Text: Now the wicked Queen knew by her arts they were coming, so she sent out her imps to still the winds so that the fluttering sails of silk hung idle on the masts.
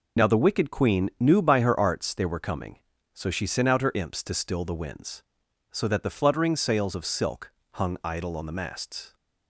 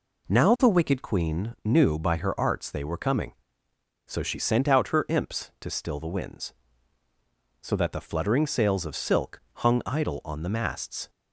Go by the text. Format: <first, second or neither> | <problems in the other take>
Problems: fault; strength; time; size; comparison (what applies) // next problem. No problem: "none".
second | loses the start of "Now"; at 0.1 s; 70 ms // pauses between "silk" and "hung"; slight; at 7.4 s; 0.22 s long